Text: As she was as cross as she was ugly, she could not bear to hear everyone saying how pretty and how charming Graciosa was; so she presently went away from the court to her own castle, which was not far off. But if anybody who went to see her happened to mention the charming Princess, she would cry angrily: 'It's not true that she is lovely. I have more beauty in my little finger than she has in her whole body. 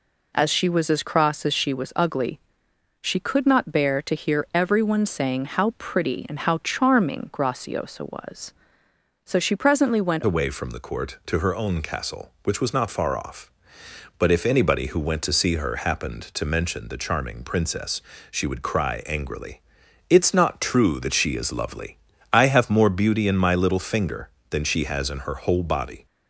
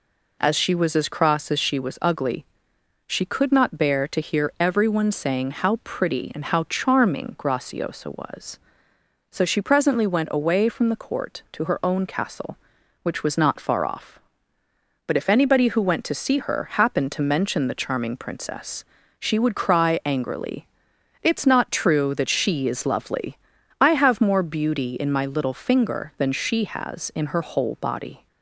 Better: second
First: changes voice at "away"; from 10.2 s on; 15.8 s long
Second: none

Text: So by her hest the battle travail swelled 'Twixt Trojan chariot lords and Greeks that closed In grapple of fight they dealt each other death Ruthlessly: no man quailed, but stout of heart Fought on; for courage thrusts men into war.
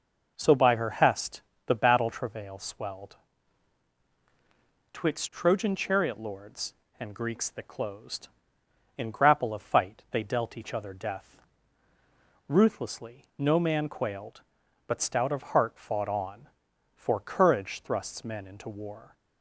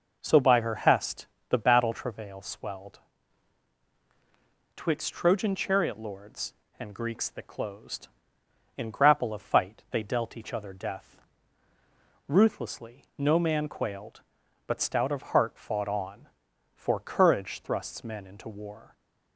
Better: neither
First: pauses between "hest" and "the"; slight; at 1.4 s; 0.26 s long // pauses between "swelled" and "Twixt"; strong; at 3.1 s; 1.7 s long // pauses between "death" and "Ruthlessly"; at 11.3 s; 1.0 s long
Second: pauses between "hest" and "the"; slight; at 1.2 s; 0.24 s long // pauses between "swelled" and "Twixt"; strong; at 2.9 s; 1.7 s long // pauses between "death" and "Ruthlessly"; at 11.1 s; 1.0 s long

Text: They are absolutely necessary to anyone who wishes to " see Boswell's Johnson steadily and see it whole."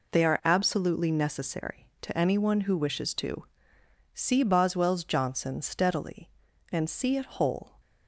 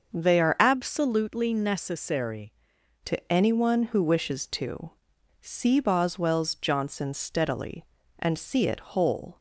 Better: first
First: none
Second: starts louder than the rest; until 1.1 s; 6.5 dB // changes voice from "absolutely" to "necessary"; from 0.5 to 2.5 s; 2.0 s long

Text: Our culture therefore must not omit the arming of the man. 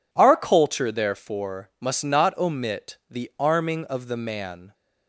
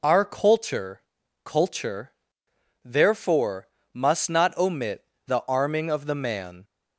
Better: first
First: none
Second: says "culture" twice; at 1.4 s // pauses between "therefore" and "must"; slight; at 3.6 s; 0.26 s long // pauses between "omit" and "the"; slight; at 5.0 s; 0.22 s long

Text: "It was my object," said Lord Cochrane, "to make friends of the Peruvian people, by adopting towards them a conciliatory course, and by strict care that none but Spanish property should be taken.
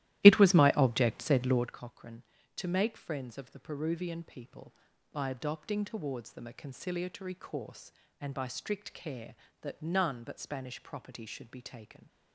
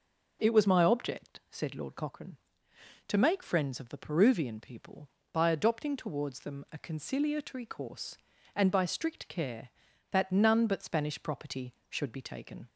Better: second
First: starts louder than the rest; strong; until 1.8 s; 15 dB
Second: none

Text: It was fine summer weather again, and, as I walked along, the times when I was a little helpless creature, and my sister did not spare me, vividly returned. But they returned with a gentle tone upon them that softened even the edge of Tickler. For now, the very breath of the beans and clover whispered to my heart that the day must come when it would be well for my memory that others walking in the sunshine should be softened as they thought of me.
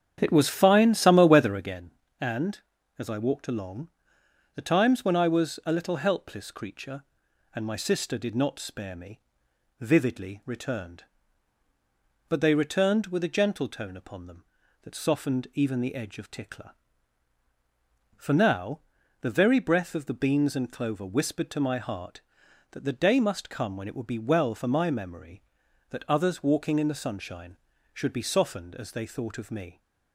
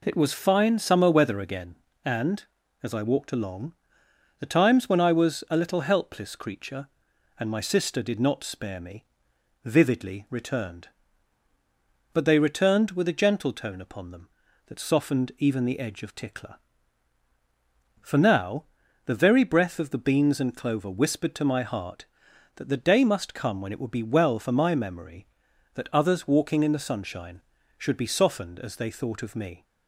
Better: second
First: starts louder than the rest; strong; until 1.7 s; 8.5 dB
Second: none

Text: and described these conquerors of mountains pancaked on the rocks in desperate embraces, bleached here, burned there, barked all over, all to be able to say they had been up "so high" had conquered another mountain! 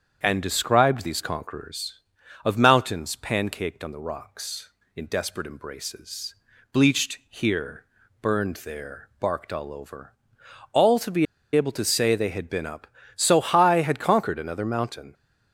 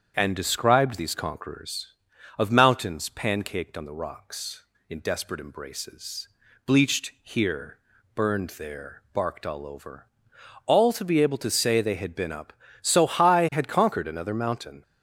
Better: second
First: starts louder than the rest; strong; until 1.2 s; 8 dB // pauses between "be" and "able"; slight; at 11.2 s; 0.30 s long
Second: starts louder than the rest; strong; until 1.1 s; 8 dB

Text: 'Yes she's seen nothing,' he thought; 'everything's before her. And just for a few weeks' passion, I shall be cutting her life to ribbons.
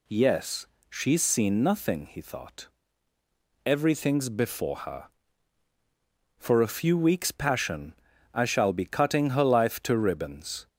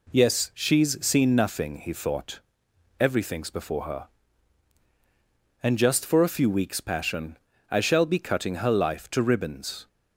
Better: second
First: pauses between "Yes" and "she's"; slight; at 0.6 s; 0.20 s long // skips "And just"; at 5.7 s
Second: none

